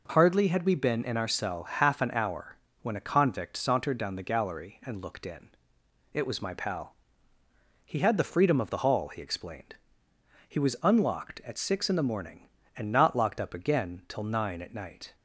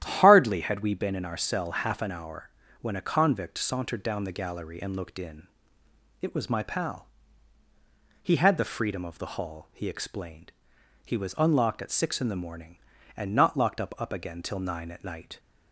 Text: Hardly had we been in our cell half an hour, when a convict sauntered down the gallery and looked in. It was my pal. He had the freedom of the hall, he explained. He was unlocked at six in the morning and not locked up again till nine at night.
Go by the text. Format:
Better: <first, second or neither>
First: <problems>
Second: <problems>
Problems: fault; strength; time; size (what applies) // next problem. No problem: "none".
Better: first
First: none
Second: starts louder than the rest; strong; until 1.0 s; 11 dB // says "up" twice; at 13.9 s